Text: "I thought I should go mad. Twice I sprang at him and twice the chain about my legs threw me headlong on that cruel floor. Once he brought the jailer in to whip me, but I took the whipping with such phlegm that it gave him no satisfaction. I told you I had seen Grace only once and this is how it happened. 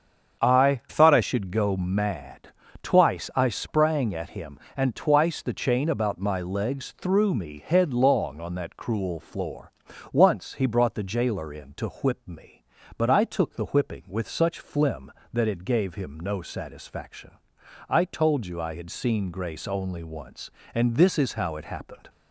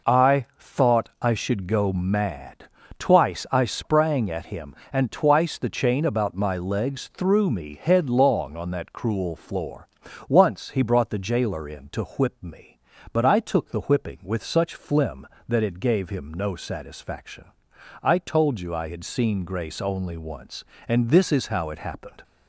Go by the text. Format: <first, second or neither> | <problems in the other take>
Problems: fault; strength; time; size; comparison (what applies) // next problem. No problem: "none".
second | starts louder than the rest; strong; until 1.5 s; 7.5 dB // changes voice from "thought" to "I"; from 0.8 to 1.2 s; 0.4 s long